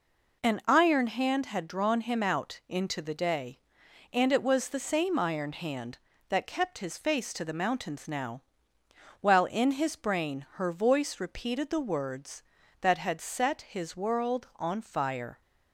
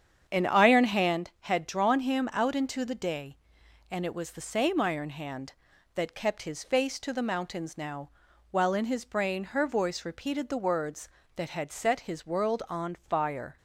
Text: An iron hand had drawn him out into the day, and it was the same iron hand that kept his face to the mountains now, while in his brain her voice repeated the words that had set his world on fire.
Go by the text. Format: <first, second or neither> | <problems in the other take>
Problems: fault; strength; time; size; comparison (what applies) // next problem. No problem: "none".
first | starts louder than the rest; strong; until 1.2 s; 8 dB